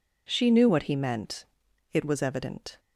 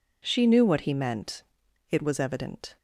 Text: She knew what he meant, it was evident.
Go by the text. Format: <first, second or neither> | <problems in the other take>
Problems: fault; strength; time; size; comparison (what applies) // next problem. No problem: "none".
neither | none